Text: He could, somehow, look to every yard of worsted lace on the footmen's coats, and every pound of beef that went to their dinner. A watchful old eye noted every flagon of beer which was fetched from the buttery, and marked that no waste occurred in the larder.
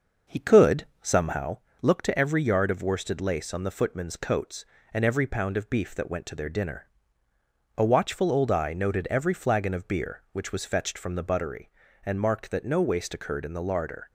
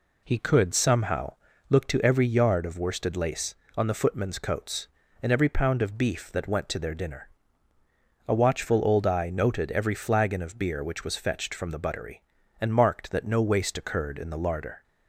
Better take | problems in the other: second | starts louder than the rest; noticeable; until 1.5 s; 6 dB

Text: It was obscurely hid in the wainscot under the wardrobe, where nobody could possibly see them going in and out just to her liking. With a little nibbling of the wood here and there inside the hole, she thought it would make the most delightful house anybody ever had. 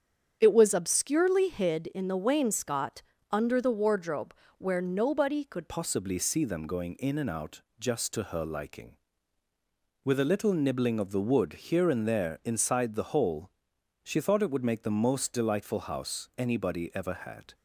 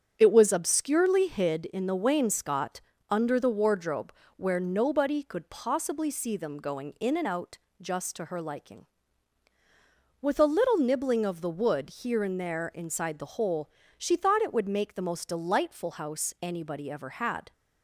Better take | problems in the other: second | starts louder than the rest; strong; until 1.4 s; 8 dB; strong in the second // pauses between "wainscot" and "under"; slight; at 3.0 s; 0.30 s long; slight in the second // changes voice at "possibly"; from 5.6 s on; 11.9 s long // pauses between "out" and "just"; slight; at 7.6 s; 0.16 s long; slight in the second // pauses between "wood" and "here"; slight; at 11.5 s; 0.18 s long

